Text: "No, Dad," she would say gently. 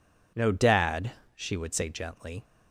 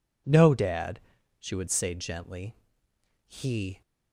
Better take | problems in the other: first | goes on to say "He"; from 3.2 s on; 0.54 s long

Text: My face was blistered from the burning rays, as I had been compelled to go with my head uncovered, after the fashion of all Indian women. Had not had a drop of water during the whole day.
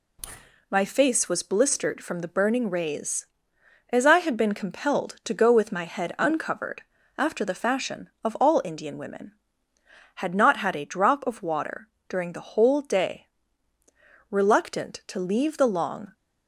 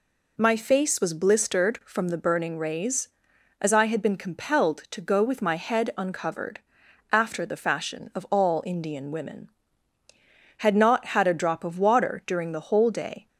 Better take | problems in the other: second | pauses between "water" and "during"; slight; at 11.8 s; 0.20 s long // goes on to say "Reluctant to leave the long"; strong; from 14.2 s on; 1.8 s long

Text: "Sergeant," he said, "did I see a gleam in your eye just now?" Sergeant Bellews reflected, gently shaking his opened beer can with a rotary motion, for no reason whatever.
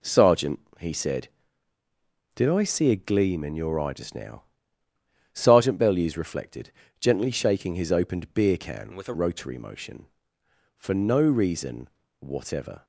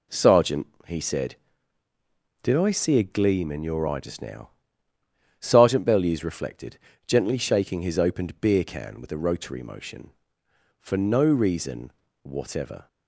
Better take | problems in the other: second | changes voice from "with" to "a"; from 8.9 to 9.1 s; 0.2 s long // pauses between "reason" and "whatever"; slight; at 11.8 s; 0.32 s long; slight in the second

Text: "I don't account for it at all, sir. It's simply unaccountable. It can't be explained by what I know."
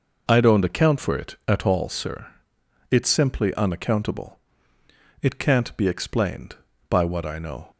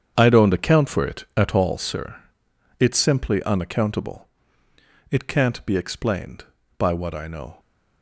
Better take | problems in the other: first | gets quieter; strong; throughout; 12 dB

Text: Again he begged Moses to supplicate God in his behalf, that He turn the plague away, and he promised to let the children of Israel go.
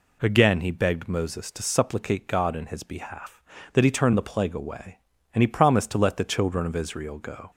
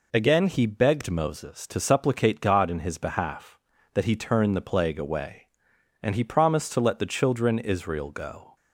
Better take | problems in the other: first | skips "of"; at 7.5 s

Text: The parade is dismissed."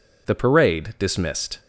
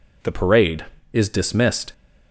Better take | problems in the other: second | skips "is"; at 0.9 s

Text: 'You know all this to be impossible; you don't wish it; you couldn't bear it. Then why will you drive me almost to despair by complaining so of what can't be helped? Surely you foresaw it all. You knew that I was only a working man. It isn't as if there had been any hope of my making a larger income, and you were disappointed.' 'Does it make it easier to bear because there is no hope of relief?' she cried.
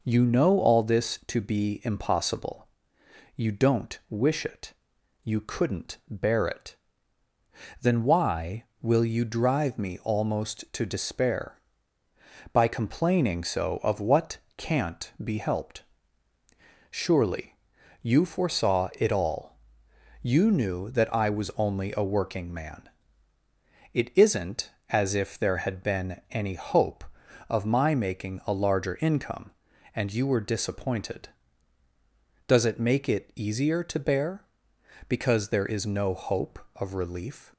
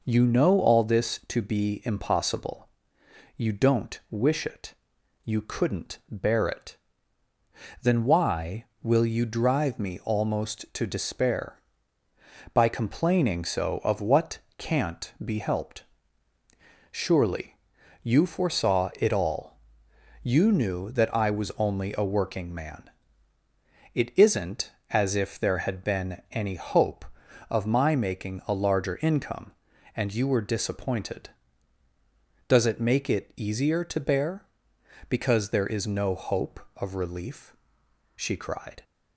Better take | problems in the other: second | pauses between "what" and "can't"; slight; at 14.3 s; 0.18 s long; slight in the second // pauses between "Surely" and "you"; at 17.5 s; 0.44 s long; also in the second // stops before "she cried"; at 37.5 s

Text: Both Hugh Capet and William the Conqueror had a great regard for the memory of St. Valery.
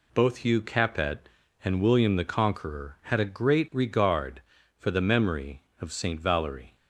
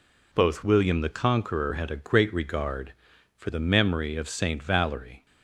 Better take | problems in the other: first | skips "Hugh Capet and"; at 0.6 s

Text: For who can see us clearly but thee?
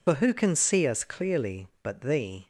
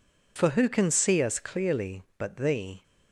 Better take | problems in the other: second | loses the start of "For"; at 0.0 s; 65 ms

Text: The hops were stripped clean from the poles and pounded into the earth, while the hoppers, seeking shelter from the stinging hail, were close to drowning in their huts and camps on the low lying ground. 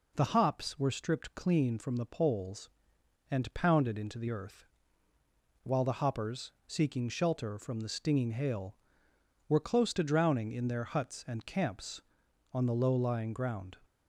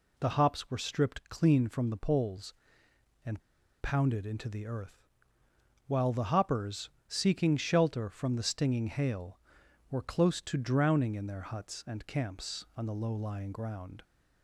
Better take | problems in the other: first | pauses between "and" and "pounded"; at 3.4 s; 0.41 s long

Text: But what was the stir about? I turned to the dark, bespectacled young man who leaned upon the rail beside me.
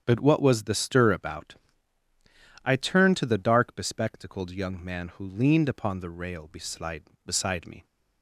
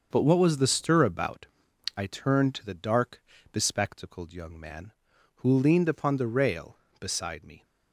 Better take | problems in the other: second | starts louder than the rest; strong; until 1.0 s; 8 dB; also in the second // says "beside" twice; at 7.2 s

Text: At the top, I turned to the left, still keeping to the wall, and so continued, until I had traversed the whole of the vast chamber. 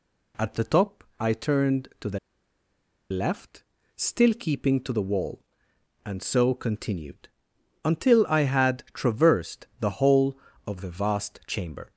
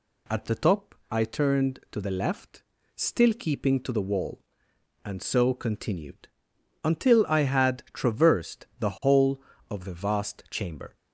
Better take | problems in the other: second | pauses between "the" and "left"; noticeable; at 2.1 s; 0.92 s long

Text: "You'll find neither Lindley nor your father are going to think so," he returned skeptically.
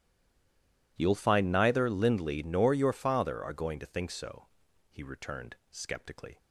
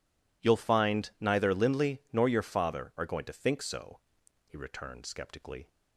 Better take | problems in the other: second | stays silent before the first word; slight; until 0.9 s; 0.9 s long

